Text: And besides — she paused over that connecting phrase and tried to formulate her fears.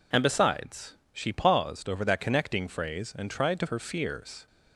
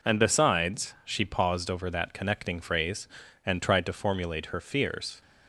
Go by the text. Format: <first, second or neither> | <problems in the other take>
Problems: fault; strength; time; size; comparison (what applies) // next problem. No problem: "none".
second | skips "formulate"; at 3.6 s